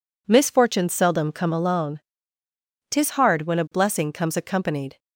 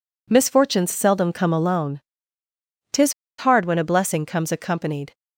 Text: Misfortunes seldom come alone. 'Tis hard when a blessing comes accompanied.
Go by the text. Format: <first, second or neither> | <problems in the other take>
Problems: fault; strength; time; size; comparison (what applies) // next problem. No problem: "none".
first | pauses between "Tis" and "hard"; slight; at 3.1 s; 0.25 s long